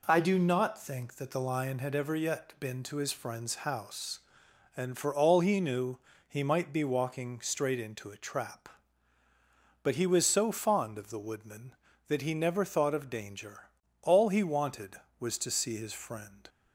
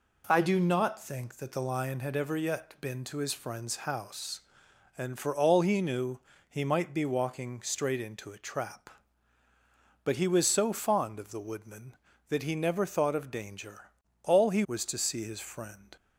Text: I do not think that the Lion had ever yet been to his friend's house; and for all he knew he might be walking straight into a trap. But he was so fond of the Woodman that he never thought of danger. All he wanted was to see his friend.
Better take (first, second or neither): first